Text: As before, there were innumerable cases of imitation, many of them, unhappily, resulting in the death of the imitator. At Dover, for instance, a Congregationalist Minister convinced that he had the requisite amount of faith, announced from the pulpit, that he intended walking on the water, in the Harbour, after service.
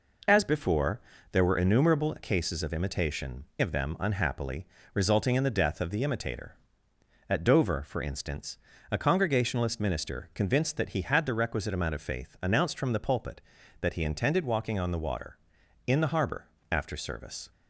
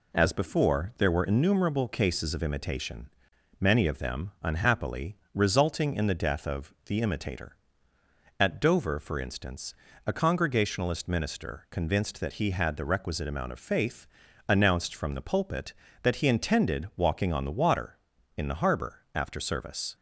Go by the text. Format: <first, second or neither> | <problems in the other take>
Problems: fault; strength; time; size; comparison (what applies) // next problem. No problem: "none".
second | skips "many"; at 3.5 s